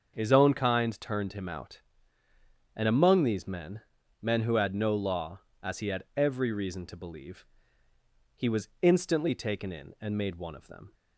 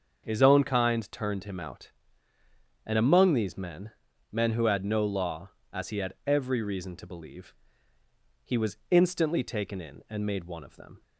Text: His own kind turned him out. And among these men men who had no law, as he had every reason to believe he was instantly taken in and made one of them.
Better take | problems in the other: neither | starts louder than the rest; the same in both // pauses between "men" and "men"; the same in both // pauses between "believe" and "he"; noticeable; the same in both

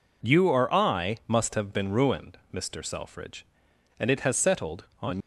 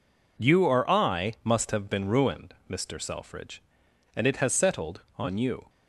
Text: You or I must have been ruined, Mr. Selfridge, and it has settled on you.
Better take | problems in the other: second | stops before "you"; at 5.2 s

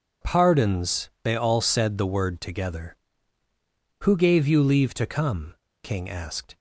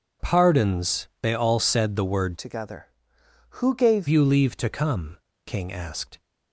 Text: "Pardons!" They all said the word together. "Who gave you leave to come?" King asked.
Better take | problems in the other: first | changes voice from "together" to "gave"; from 2.3 to 4.0 s; 1.7 s long

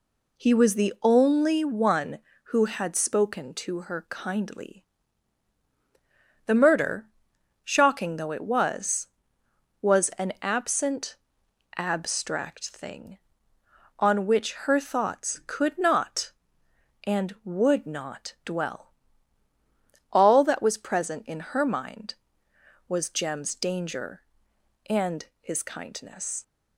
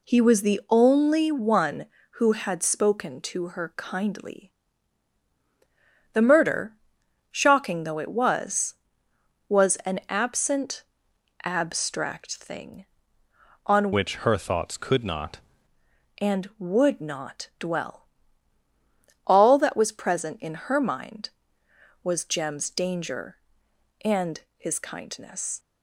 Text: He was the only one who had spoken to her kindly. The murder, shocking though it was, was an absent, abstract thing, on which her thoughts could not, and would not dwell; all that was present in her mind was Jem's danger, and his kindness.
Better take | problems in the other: first | changes voice from "which" to "not"; from 13.9 to 15.3 s; 1.4 s long // pauses between "and" and "his"; slight; at 24.3 s; 0.18 s long; slight in the first

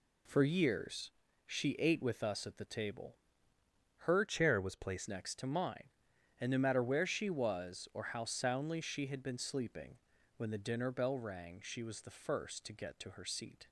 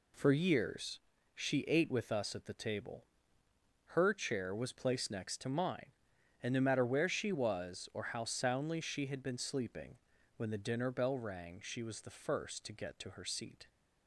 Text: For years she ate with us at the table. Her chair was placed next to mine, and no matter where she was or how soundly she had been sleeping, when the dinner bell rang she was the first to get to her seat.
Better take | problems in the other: second | pauses between "years" and "she"; slight; at 1.1 s; 0.34 s long; slight in the second // changes voice from "chair" to "placed"; from 4.2 to 5.0 s; 0.8 s long

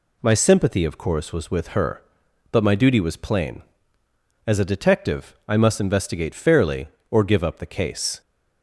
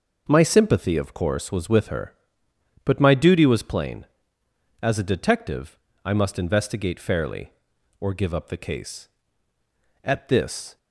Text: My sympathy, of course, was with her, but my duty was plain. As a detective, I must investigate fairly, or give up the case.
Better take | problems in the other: first | goes on to say "At this"; noticeable; from 10.0 s on; 0.74 s long

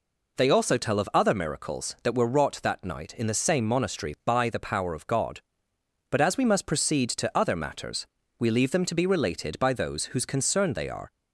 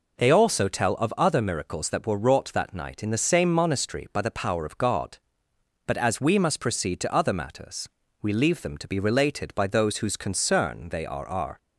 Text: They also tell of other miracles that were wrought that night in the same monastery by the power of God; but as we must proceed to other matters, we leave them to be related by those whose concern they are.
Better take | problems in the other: first | says "are" twice; at 11.2 s

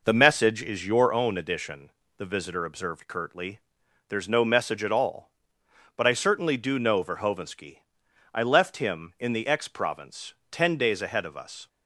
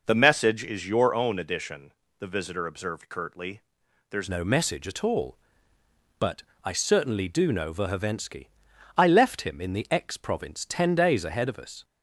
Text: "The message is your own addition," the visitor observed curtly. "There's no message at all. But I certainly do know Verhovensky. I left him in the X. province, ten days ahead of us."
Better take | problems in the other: first | changes voice at "no"; from 4.2 s on; 7.6 s long // pauses between "But" and "I"; slight; at 6.4 s; 0.20 s long

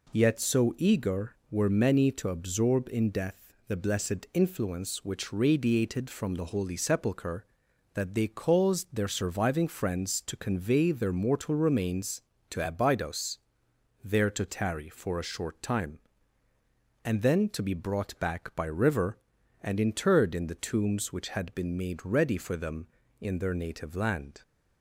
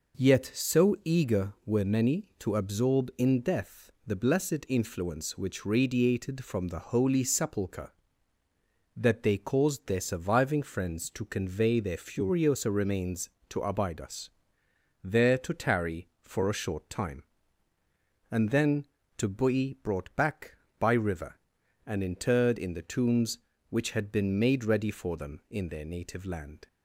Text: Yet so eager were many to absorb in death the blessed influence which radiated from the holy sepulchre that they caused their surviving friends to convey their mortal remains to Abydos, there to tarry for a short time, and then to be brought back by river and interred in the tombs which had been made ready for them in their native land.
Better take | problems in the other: first | says "furiosa" for "mortal"; at 11.9 s

